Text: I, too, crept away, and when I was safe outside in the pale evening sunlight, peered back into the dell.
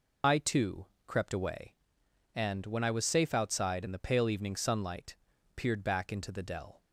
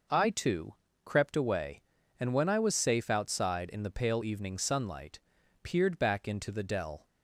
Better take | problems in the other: second | loses the start of "I"; at 0.2 s; 85 ms

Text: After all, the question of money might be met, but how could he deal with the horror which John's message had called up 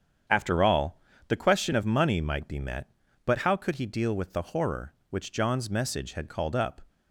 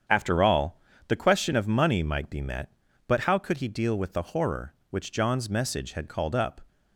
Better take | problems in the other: neither | starts louder than the rest; strong; the same in both

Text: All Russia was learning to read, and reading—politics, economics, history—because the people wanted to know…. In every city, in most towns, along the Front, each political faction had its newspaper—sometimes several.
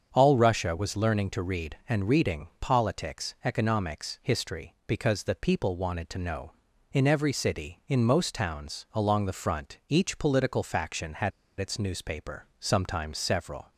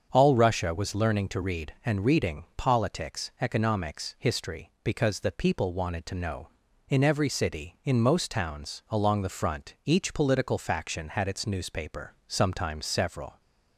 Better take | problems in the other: second | starts louder than the rest; strong; until 1.1 s; 7 dB; also in the second // pauses between "had" and "its"; slight; at 11.3 s; 0.27 s long

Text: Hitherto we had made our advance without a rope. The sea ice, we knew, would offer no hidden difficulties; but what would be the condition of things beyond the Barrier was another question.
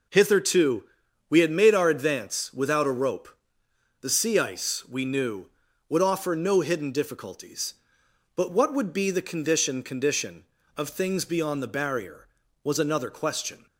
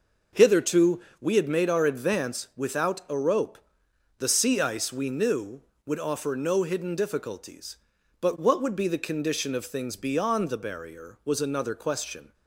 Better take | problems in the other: second | pauses between "Hitherto" and "we"; at 0.8 s; 0.44 s long; slight in the second // says "condition" twice; at 9.8 s

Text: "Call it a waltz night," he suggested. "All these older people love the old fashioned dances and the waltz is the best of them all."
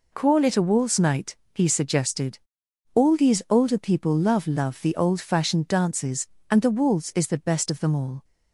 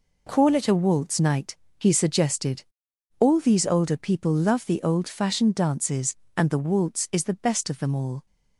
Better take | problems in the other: second | says "love" twice; at 4.4 s

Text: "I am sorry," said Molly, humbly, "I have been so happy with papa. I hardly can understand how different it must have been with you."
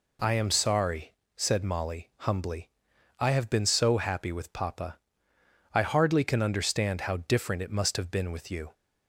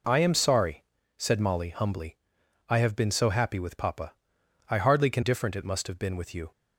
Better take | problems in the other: first | skips "understand how"; at 5.2 s

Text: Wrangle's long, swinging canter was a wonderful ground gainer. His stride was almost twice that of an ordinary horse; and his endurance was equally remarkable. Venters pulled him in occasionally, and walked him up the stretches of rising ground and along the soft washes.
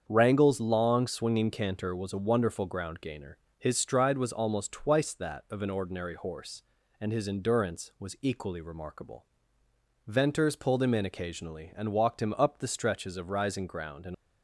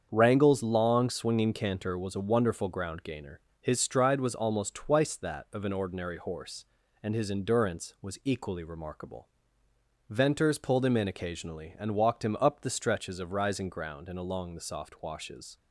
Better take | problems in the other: second | starts louder than the rest; strong; until 1.0 s; 7.5 dB; strong in the second // stops before "along the soft washes"; at 14.1 s

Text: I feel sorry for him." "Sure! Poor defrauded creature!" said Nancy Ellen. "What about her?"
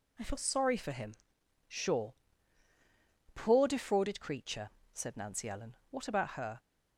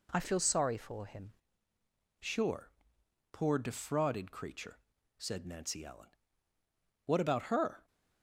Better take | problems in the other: first | changes voice at "Sure"; from 2.2 s on; 5.6 s long

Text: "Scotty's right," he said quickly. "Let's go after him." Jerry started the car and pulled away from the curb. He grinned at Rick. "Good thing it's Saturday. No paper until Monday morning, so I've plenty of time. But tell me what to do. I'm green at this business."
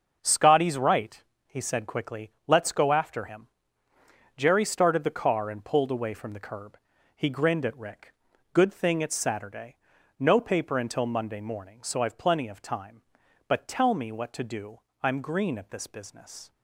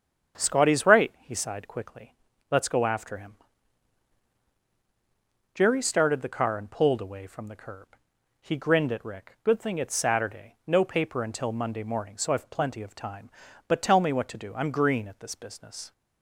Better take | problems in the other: first | starts louder than the rest; strong; until 1.4 s; 7 dB; also in the first // says "sighed" for "said"; at 1.3 s

